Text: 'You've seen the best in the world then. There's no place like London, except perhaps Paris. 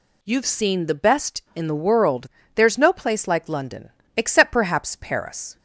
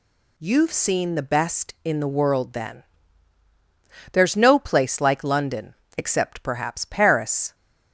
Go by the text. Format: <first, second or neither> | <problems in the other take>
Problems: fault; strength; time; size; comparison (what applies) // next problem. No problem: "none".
second | skips "then"; at 2.3 s